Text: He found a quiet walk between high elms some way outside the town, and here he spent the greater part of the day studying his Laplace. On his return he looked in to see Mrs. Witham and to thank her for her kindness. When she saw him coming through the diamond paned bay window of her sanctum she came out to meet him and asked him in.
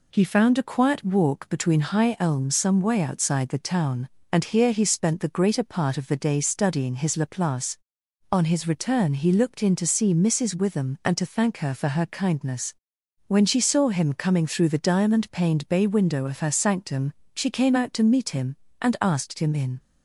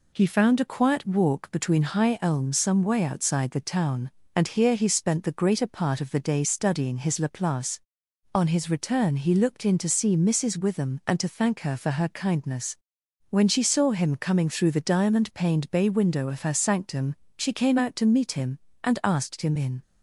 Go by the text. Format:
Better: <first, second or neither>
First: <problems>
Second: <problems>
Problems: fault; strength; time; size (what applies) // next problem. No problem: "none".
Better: neither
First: pauses between "sanctum" and "she"; slight; at 17.1 s; 0.22 s long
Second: pauses between "sanctum" and "she"; slight; at 17.1 s; 0.22 s long